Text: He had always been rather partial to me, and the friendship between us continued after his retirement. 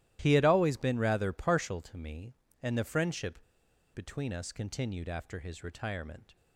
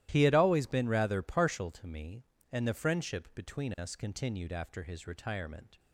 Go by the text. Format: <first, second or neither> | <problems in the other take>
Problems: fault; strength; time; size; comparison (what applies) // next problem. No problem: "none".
second | starts louder than the rest; strong; until 1.2 s; 14 dB; strong in the second // pauses between "friendship" and "between"; noticeable; at 3.4 s; 0.53 s long